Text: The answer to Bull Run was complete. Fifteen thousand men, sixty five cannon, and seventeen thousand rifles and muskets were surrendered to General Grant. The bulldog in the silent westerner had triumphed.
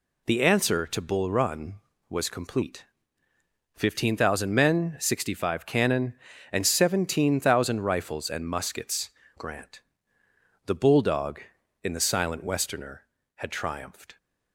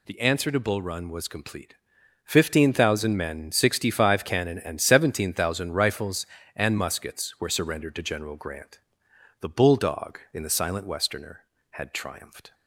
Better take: second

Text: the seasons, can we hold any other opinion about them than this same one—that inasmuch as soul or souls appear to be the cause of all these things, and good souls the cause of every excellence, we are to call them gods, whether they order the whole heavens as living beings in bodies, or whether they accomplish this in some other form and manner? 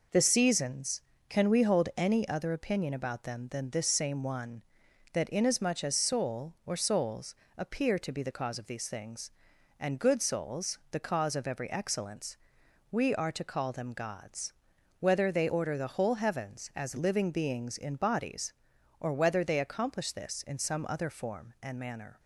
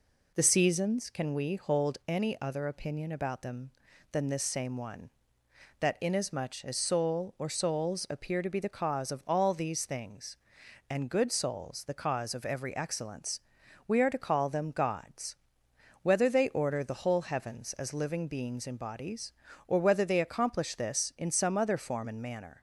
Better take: second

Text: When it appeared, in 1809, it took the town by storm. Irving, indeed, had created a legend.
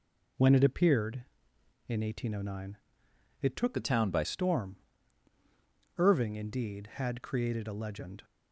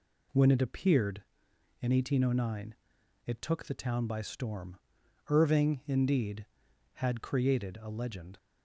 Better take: second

